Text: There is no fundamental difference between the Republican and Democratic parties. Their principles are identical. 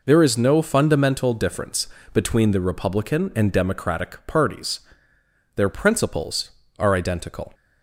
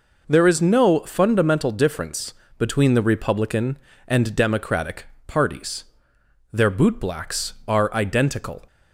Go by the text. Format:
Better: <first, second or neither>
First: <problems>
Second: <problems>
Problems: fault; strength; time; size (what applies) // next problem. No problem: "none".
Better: first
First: pauses between "difference" and "between"; slight; at 1.8 s; 0.26 s long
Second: pauses between "difference" and "between"; slight; at 2.3 s; 0.24 s long // pauses between "Democratic" and "parties"; slight; at 5.0 s; 0.22 s long // says "bootblacks" for "principles"; at 6.7 s